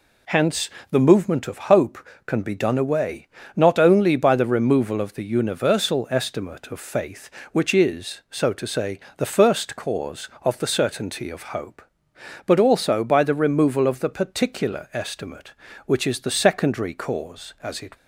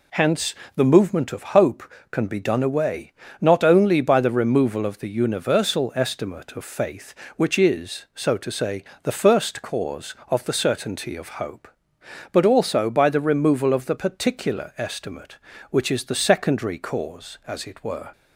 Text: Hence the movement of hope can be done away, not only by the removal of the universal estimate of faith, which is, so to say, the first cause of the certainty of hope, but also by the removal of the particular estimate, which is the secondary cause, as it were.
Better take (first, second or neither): second